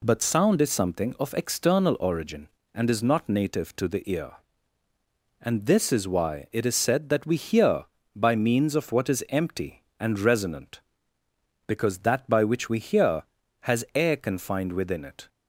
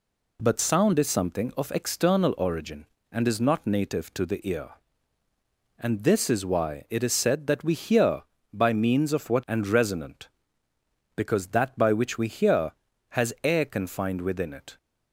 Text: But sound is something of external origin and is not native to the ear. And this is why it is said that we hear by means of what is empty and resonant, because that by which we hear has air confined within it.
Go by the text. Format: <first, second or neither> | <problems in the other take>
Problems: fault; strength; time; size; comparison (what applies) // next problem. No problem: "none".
first | skips "is empty"; at 9.4 s